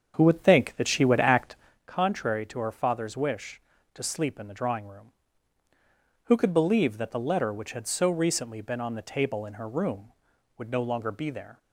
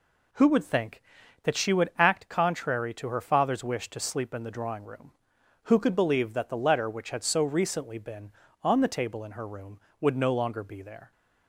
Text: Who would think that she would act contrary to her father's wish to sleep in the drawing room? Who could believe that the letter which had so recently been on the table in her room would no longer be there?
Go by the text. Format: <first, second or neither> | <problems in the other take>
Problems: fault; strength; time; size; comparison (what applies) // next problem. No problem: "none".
second | starts louder than the rest; strong; until 1.8 s; 7.5 dB // pauses between "act" and "contrary"; slight; at 1.5 s; 0.30 s long